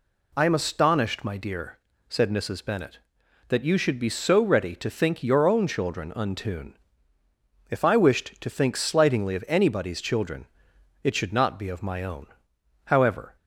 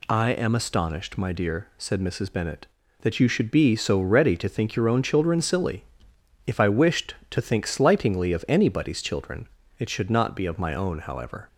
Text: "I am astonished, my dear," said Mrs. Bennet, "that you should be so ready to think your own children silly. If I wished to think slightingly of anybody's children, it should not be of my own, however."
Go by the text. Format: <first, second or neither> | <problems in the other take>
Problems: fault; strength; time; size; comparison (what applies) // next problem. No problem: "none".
second | says "untune" for "silly"; at 6.1 s